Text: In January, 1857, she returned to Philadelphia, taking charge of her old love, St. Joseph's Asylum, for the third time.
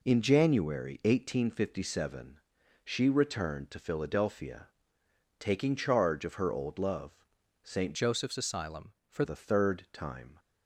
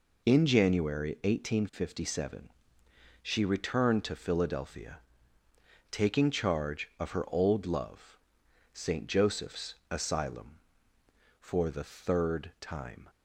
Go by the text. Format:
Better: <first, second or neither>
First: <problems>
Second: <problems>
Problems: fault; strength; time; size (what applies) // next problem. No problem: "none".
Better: second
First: changes voice from "Joseph's" to "for"; from 7.9 to 9.2 s; 1.3 s long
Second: none